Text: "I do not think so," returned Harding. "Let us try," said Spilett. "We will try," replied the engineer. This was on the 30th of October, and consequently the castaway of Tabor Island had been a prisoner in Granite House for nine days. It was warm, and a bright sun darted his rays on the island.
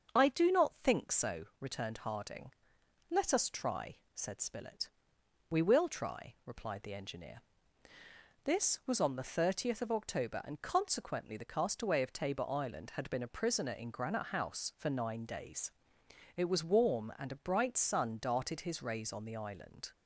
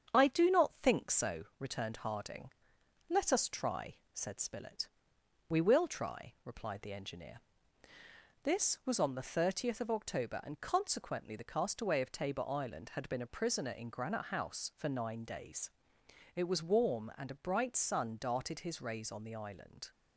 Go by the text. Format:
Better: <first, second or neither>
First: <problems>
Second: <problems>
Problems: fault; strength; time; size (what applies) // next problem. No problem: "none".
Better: first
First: starts louder than the rest; until 1.2 s; 6.5 dB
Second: gets quieter; slight; throughout; 3 dB // starts louder than the rest; strong; until 1.2 s; 7.5 dB